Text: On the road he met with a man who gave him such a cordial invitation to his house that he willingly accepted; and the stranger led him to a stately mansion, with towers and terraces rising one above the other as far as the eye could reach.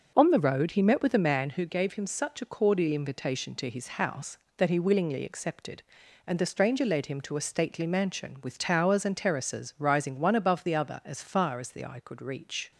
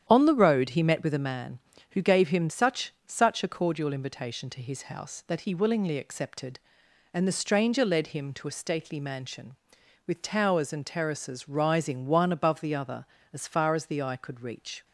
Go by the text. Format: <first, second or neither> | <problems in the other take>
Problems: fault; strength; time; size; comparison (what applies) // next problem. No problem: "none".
first | starts louder than the rest; strong; until 1.0 s; 9.5 dB; noticeable in the first // says "such" twice; at 3.0 s